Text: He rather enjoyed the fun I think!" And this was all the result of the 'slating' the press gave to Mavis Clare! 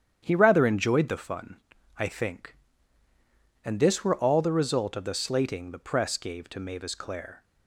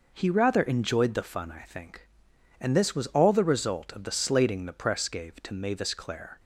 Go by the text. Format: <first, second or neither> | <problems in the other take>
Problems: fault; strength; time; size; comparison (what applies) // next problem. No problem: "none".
second | starts louder than the rest; strong; until 1.2 s; 9 dB // pauses between "fun" and "I"; at 1.5 s; 0.40 s long // says "were" for "was"; at 4.0 s